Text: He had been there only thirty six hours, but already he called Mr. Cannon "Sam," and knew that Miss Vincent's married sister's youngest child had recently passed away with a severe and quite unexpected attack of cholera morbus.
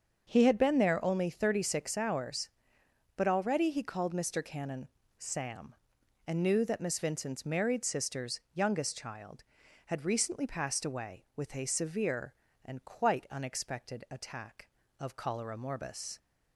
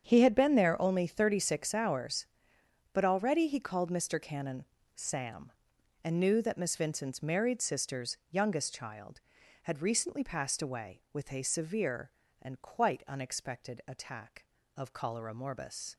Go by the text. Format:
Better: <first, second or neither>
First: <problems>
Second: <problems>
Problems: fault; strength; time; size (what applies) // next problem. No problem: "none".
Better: first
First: starts louder than the rest; until 1.3 s; 6.5 dB // pauses between "Cannon" and "Sam"; slight; at 4.8 s; 0.30 s long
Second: gets quieter; strong; throughout; 14.5 dB // starts louder than the rest; strong; until 1.0 s; 7.5 dB // pauses between "Cannon" and "Sam"; slight; at 4.6 s; 0.30 s long